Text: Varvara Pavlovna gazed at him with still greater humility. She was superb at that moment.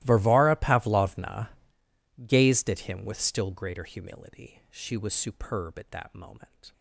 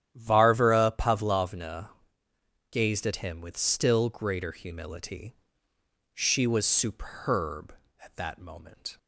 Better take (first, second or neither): second